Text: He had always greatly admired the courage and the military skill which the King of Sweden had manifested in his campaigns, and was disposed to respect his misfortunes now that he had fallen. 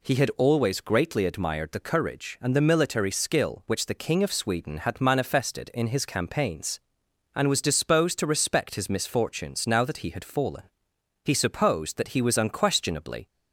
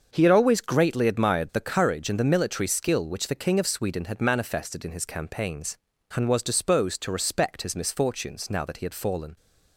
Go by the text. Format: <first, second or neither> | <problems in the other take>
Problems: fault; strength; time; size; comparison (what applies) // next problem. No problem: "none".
second | goes on to say "He supposed that he was unquestionably"; strong; from 11.2 s on; 2.0 s long